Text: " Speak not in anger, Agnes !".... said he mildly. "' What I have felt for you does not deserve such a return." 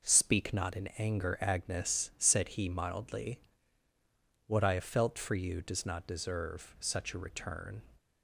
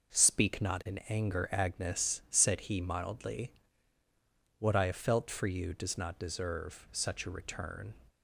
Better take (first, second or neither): neither